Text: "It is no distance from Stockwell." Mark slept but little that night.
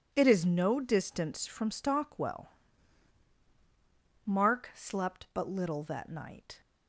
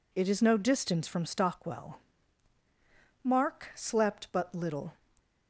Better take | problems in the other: first | stops before "that night"; at 5.1 s

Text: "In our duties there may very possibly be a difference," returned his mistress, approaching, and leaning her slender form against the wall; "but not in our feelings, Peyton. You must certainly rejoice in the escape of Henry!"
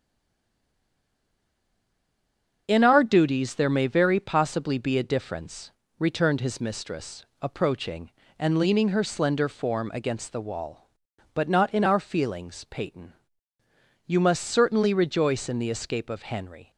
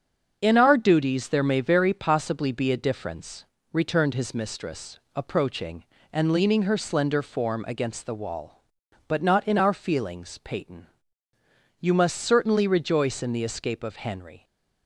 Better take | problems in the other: second | stays silent before the first word; strong; until 2.6 s; 2.6 s long // starts louder than the rest; strong; until 3.6 s; 7 dB; strong in the second

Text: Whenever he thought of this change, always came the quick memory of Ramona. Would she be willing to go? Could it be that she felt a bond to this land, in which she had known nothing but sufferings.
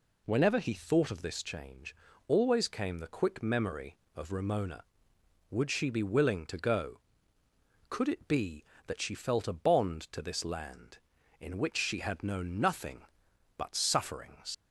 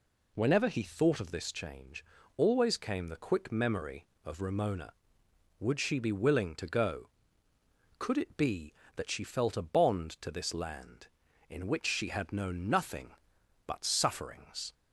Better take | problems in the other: second | leaves "sufferings" unfinished; at 14.5 s; 95 ms

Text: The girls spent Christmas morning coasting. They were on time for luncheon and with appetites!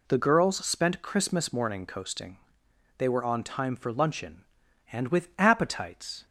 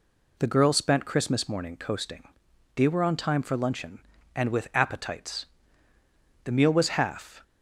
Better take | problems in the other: first | goes on to say "The meal was half"; noticeable; from 6.4 s on; 1.0 s long

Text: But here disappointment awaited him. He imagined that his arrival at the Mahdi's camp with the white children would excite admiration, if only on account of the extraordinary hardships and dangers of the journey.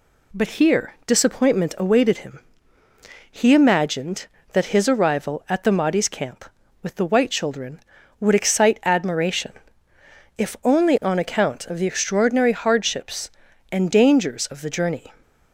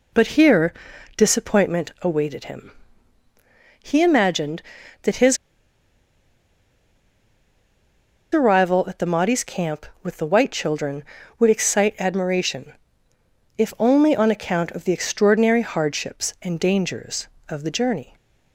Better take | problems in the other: first | pauses between "here" and "disappointment"; at 0.7 s; 0.44 s long // pauses between "his" and "arrival"; strong; at 5.3 s; 2.9 s long

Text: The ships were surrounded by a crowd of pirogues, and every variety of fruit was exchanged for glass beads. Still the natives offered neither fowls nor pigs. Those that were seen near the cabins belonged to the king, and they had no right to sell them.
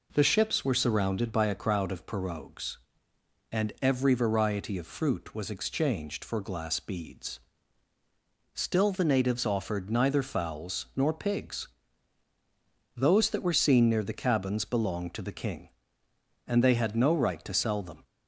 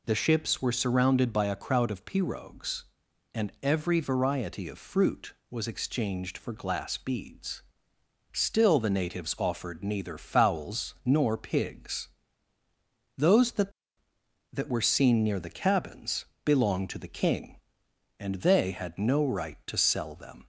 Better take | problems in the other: first | says "that" twice; at 14.5 s // pauses between "cabins" and "belonged"; slight; at 16.2 s; 0.20 s long

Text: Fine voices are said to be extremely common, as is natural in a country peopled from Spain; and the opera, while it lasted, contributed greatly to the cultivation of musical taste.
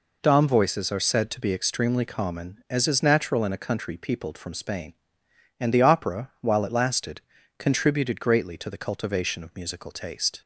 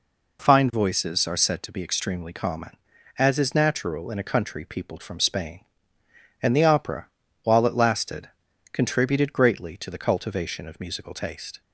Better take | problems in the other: second | says "Dom" for "Fine"; at 0.2 s

